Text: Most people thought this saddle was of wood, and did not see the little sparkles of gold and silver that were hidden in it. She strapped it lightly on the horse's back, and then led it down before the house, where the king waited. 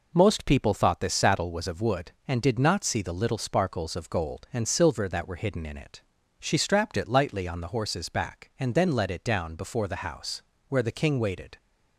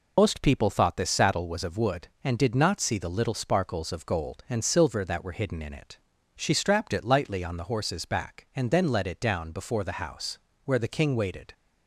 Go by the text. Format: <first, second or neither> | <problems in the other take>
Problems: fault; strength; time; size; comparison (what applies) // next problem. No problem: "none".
first | loses the start of "Most"; at 0.1 s; 80 ms